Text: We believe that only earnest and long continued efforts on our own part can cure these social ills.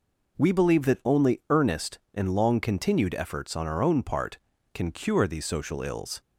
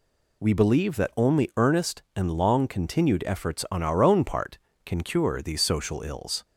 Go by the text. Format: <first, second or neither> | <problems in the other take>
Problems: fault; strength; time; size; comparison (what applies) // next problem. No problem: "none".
neither | none